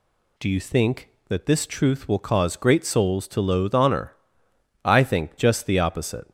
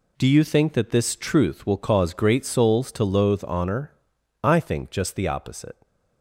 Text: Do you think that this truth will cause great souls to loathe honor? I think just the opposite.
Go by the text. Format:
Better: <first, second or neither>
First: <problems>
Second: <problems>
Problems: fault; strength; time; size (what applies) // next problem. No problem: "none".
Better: first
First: none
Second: gets quieter; strong; throughout; 10 dB